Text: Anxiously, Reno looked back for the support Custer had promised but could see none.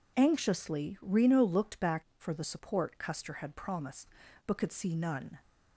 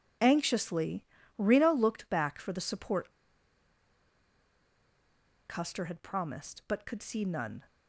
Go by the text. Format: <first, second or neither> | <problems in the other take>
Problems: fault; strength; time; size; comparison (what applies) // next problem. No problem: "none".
first | pauses between "support" and "Custer"; strong; at 3.1 s; 2.3 s long